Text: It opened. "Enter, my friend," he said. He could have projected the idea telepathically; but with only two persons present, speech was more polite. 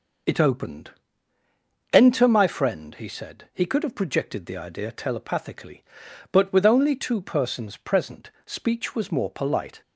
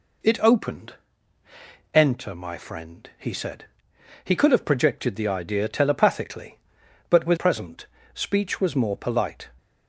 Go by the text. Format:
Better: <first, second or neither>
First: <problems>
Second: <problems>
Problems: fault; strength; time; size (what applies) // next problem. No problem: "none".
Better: first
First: none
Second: skips "only two persons"; at 7.3 s